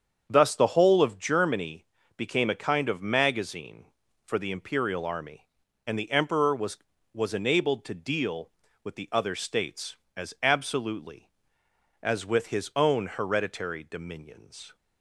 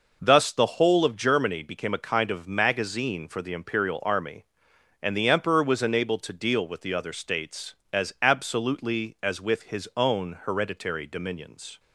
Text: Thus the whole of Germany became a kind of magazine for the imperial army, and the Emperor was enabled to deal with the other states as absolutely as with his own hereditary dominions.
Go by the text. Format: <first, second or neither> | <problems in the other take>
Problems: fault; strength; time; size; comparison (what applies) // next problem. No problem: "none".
second | starts louder than the rest; strong; until 1.3 s; 7.5 dB // pauses between "Germany" and "became"; slight; at 1.8 s; 0.32 s long // says "was" twice; at 7.1 s